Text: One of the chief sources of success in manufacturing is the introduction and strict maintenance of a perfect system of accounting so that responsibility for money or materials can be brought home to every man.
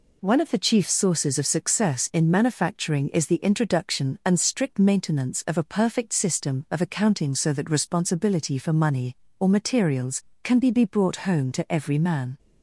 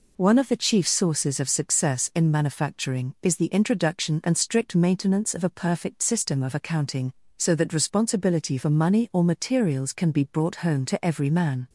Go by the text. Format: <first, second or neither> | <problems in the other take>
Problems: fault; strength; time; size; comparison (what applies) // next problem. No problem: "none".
second | says "be" twice; at 10.6 s